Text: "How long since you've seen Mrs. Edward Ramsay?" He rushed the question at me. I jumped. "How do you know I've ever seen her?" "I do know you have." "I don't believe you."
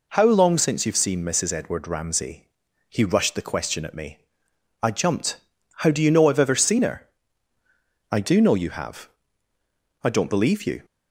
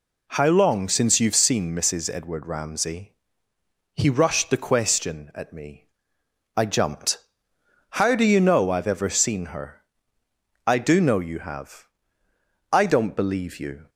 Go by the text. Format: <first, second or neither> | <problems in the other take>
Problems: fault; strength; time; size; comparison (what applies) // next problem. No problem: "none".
neither | none